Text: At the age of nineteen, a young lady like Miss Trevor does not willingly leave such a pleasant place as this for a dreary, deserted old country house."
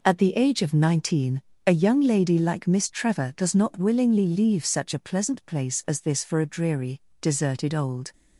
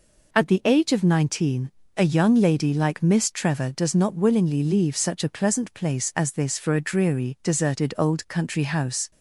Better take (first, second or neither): second